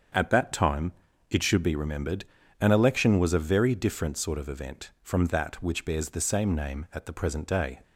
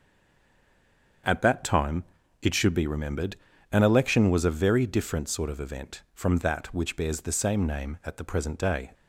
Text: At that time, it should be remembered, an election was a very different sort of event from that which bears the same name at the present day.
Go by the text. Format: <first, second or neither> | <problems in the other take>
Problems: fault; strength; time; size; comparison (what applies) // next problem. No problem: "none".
first | stays silent before the first word; noticeable; until 1.2 s; 1.2 s long // starts louder than the rest; strong; until 2.6 s; 7 dB; strong in the first